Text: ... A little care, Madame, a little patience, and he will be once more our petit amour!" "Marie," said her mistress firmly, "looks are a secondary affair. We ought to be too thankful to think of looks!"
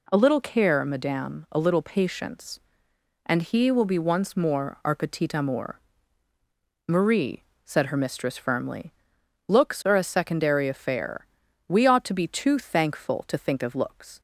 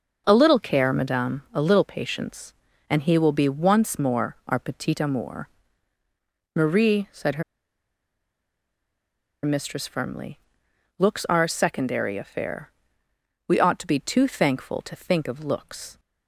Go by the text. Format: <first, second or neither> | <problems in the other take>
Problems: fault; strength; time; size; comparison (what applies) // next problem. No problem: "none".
first | starts louder than the rest; until 1.2 s; 6 dB // pauses between "her" and "mistress"; strong; at 7.4 s; 2.0 s long